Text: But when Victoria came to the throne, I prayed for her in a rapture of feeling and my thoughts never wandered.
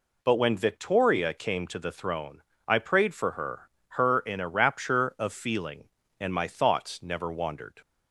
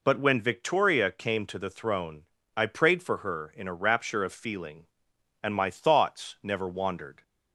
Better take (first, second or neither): second